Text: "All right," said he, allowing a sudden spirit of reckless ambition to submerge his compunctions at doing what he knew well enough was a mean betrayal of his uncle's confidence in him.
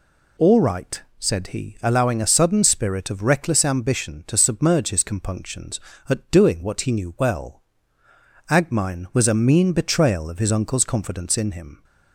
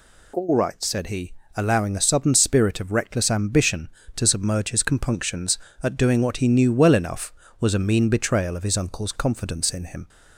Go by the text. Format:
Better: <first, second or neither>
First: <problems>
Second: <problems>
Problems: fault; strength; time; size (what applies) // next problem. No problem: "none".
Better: second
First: says "agmine" for "enough"; at 8.4 s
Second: none